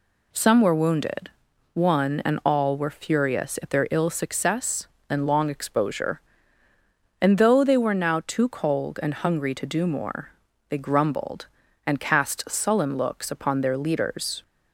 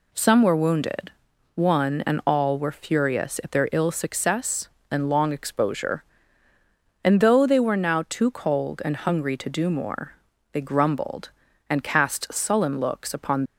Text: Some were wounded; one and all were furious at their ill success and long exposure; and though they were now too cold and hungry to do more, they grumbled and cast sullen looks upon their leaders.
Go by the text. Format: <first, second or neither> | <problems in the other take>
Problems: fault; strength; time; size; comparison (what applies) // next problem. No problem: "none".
first | stops before "their leaders"; at 13.4 s